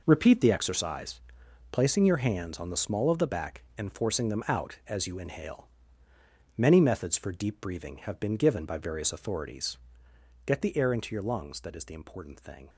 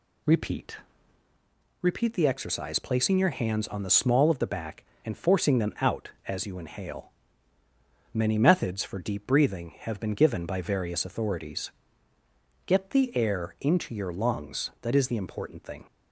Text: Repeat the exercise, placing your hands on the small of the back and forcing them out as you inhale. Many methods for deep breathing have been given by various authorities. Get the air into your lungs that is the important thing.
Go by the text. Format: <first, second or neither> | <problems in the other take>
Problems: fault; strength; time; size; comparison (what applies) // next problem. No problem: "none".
first | says "Repeat" twice; at 1.8 s